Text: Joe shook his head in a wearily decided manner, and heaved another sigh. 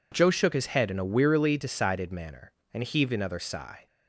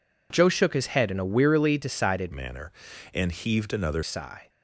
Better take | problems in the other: first | changes voice from "manner" to "another"; from 2.3 to 4.0 s; 1.7 s long

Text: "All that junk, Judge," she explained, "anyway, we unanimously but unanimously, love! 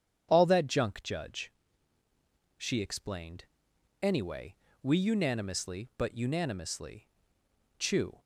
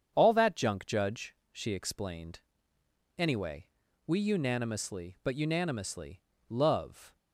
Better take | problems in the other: second | starts louder than the rest; strong; until 1.3 s; 8.5 dB; strong in the second // says "chew" for "love"; at 7.7 s

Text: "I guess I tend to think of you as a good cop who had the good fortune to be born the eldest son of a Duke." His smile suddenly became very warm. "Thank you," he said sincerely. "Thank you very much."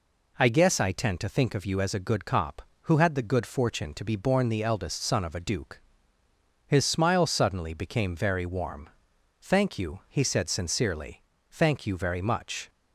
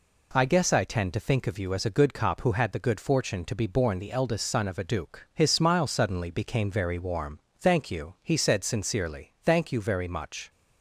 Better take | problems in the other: neither | none

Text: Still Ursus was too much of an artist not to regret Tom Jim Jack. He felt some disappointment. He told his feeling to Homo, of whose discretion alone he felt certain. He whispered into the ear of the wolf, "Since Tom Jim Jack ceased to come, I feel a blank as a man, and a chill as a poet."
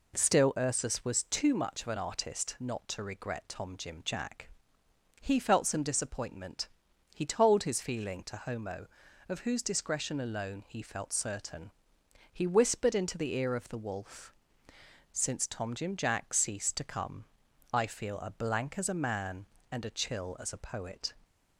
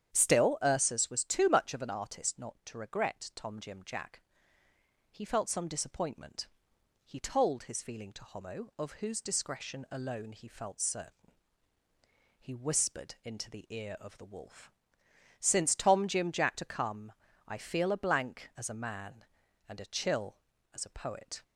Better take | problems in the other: first | starts louder than the rest; strong; until 1.1 s; 9 dB // skips "ceased"; at 16.5 s

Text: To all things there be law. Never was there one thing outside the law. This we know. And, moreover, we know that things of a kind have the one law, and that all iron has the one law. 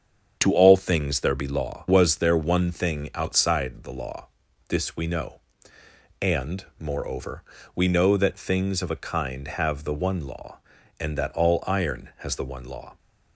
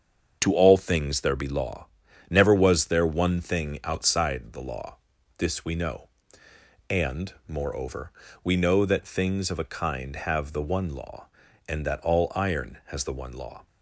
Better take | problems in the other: second | starts louder than the rest; strong; until 1.4 s; 7.5 dB; also in the second // skips "Never"; at 1.8 s

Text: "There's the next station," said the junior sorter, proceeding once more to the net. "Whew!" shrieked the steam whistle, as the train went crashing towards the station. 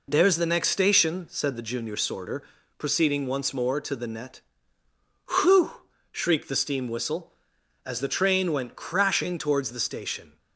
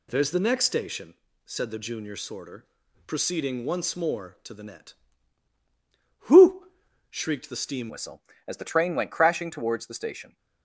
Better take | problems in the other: first | changes voice at "whistle"; from 7.8 s on; 2.5 s long

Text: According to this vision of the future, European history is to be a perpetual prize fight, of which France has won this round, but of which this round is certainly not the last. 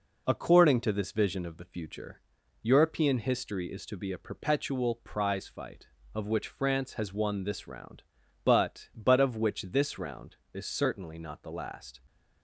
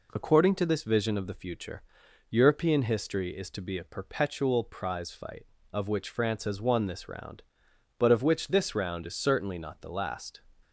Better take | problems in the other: second | says "but" twice; at 8.9 s

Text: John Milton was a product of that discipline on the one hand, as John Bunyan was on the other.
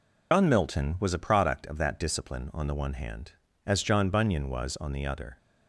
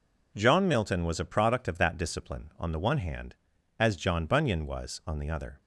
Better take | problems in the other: second | loses the start of "John"; at 0.3 s; 95 ms

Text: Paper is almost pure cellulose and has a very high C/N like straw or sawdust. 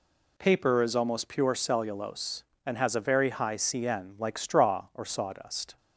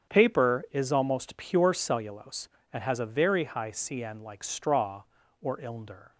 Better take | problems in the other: first | starts louder than the rest; strong; until 1.1 s; 8 dB // says "ilnder" for "sawdust"; at 5.5 s

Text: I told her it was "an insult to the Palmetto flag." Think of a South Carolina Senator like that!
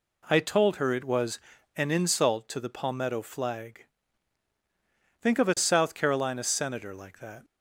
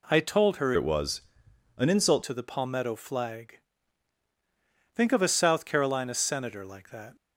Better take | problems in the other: first | changes voice from "it" to "insult"; from 0.7 to 2.2 s; 1.5 s long // pauses between "was" and "an"; noticeable; at 1.2 s; 0.56 s long; also in the first

